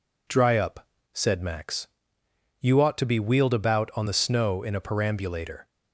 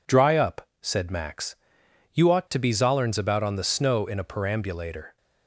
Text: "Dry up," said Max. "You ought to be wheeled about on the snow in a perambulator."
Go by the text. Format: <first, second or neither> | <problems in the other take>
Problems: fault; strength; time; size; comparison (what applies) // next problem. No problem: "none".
first | says "zollerns" for "wheeled"; at 2.7 s